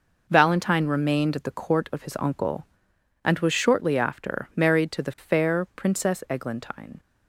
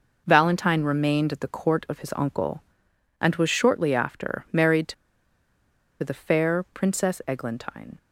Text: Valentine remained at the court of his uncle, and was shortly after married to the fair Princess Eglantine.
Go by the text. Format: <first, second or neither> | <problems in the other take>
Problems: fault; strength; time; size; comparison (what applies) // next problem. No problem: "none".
first | pauses between "to" and "the"; at 4.9 s; 1.0 s long